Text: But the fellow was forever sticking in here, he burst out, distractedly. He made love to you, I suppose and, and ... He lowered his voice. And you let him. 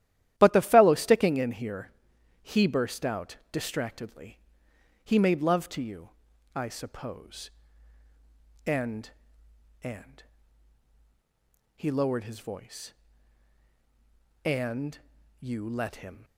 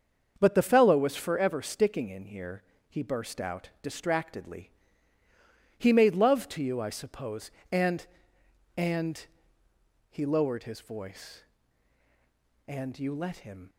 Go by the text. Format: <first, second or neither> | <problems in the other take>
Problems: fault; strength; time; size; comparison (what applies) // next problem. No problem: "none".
second | starts louder than the rest; strong; until 1.3 s; 12.5 dB; also in the second // skips "was forever"; at 0.9 s // pauses between "And" and "you"; at 14.9 s; 0.42 s long